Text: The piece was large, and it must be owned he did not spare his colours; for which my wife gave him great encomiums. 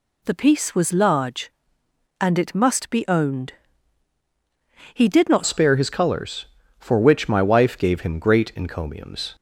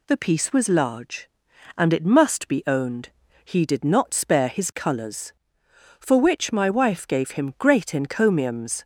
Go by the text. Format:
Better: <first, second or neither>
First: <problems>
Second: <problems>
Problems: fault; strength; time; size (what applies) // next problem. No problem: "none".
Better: second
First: pauses between "owned" and "he"; strong; at 3.5 s; 1.4 s long // changes voice at "spare"; from 5.4 s on; 3.9 s long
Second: pauses between "owned" and "he"; at 3.0 s; 0.38 s long